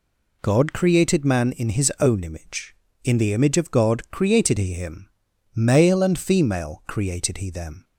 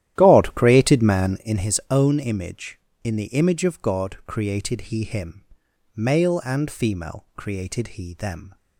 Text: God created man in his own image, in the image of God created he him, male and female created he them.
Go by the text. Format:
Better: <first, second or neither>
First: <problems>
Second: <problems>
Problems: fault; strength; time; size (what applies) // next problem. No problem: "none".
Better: first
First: none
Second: starts louder than the rest; strong; until 1.6 s; 12 dB